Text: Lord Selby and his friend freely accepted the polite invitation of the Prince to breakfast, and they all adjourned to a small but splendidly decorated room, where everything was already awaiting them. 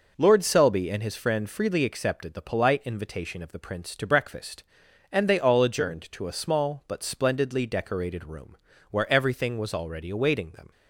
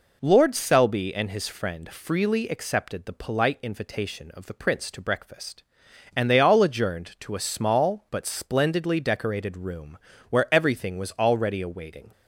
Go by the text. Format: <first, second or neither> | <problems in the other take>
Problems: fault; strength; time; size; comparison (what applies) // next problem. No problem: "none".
first | stops before "them"; at 12.1 s